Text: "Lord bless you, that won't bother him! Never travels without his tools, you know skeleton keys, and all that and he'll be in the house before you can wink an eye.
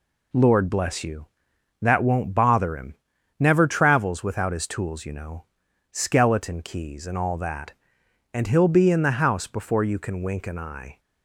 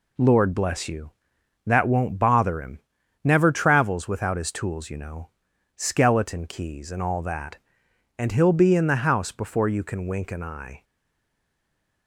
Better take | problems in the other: first | pauses between "know" and "skeleton"; noticeable; at 5.2 s; 0.46 s long; noticeable in the first // stays silent after the last word; noticeable; from 10.8 s on; 1.2 s long

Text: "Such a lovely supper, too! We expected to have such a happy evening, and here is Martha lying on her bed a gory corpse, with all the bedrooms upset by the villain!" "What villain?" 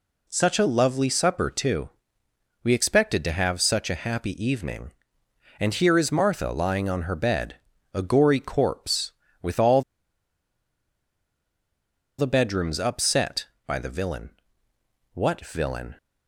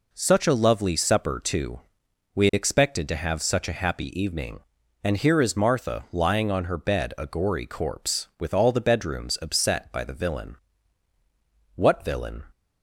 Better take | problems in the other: second | pauses between "bed" and "a"; at 7.5 s; 0.38 s long // pauses between "all" and "the"; strong; at 9.8 s; 2.3 s long

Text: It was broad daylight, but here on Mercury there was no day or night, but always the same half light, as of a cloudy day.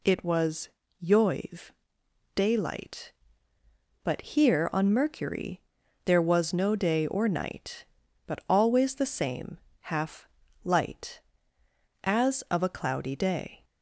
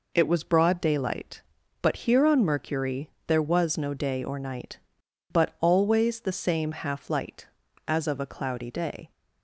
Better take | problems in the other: second | says "yoiv" for "broad"; at 1.0 s // pauses between "Mercury" and "there"; noticeable; at 5.5 s; 0.46 s long; slight in the second // pauses between "same" and "half"; slight; at 9.5 s; 0.24 s long // pauses between "half" and "light"; at 10.2 s; 0.38 s long

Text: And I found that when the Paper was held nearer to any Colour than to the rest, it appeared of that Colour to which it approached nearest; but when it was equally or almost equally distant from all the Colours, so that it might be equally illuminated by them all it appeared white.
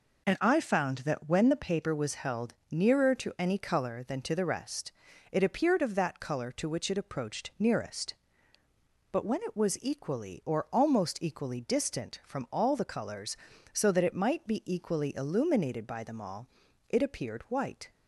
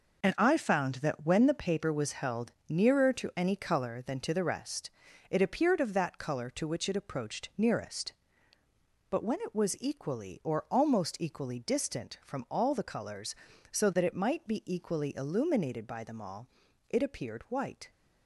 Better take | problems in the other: first | gets quieter; strong; throughout; 8.5 dB // pauses between "held" and "nearer"; slight; at 2.5 s; 0.16 s long; slight in the first // pauses between "all" and "it"; at 16.4 s; 0.40 s long; also in the first

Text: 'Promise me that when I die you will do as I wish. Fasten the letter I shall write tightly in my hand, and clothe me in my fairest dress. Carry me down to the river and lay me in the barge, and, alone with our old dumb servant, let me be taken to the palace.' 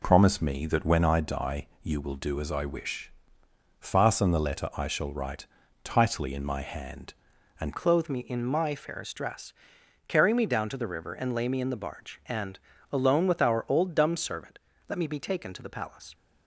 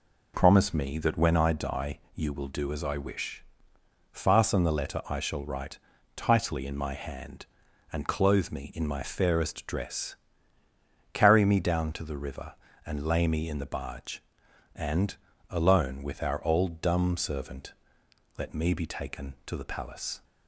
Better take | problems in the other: second | pauses between "write" and "tightly"; at 5.4 s; 0.38 s long; also in the second // changes voice at "clothe"; from 7.7 s on; 8.4 s long

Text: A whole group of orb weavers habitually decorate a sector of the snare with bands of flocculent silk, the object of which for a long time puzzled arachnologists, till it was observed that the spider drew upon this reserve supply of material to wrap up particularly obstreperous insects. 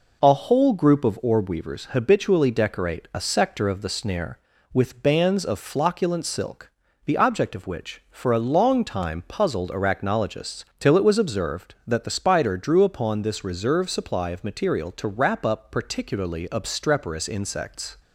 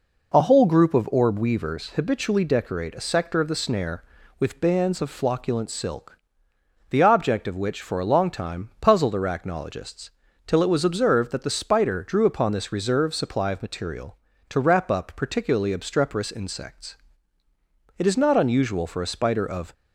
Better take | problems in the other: first | goes on to say "It is not unusual for a spider of"; strong; from 17.9 s on; 1.7 s long

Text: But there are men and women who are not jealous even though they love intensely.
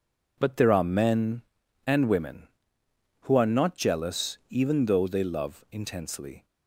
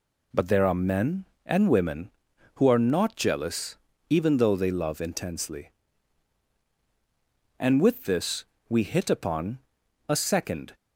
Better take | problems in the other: first | pauses between "jealous" and "even"; slight; at 3.7 s; 0.32 s long // goes on to say "And with this we hit upon a second"; strong; from 7.5 s on; 3.1 s long

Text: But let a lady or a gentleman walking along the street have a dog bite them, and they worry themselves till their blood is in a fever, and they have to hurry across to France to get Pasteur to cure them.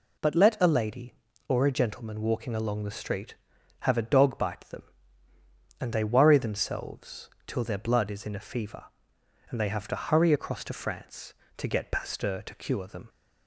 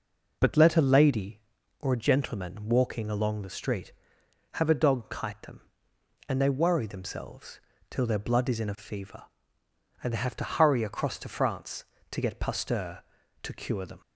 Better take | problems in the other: first | says "kite" for "bite"; at 5.0 s // pauses between "themselves" and "till"; slight; at 7.5 s; 0.32 s long; slight in the first

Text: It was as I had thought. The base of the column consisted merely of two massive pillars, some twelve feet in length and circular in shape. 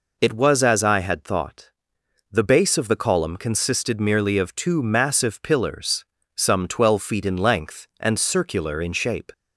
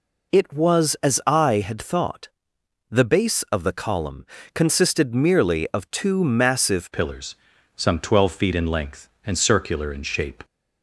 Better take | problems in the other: first | pauses between "column" and "consisted"; slight; at 4.2 s; 0.30 s long // changes voice at "pillars"; from 6.9 s on; 3.5 s long

